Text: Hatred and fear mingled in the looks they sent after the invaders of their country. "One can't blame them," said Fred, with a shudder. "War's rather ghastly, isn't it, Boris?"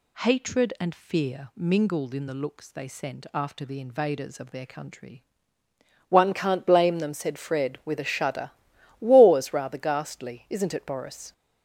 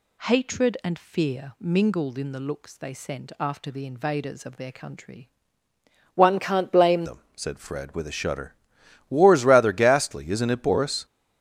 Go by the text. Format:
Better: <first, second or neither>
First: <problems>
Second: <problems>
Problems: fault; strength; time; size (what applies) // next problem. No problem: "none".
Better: first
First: none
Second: changes voice at "them"; from 7.0 s on; 4.0 s long